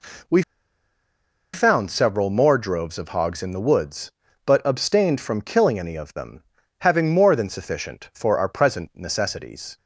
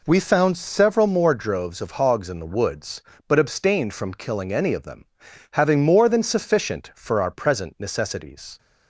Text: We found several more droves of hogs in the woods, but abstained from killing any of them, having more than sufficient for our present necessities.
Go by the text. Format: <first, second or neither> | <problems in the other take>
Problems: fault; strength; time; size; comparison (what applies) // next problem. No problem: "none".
second | pauses between "We" and "found"; at 0.4 s; 1.1 s long